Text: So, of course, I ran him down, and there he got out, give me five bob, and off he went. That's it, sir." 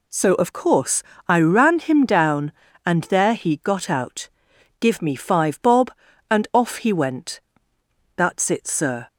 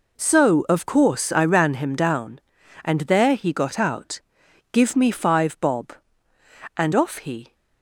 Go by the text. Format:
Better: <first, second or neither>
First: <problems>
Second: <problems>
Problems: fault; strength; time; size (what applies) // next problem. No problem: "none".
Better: first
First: none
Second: stops before "went That's it sir"; at 7.5 s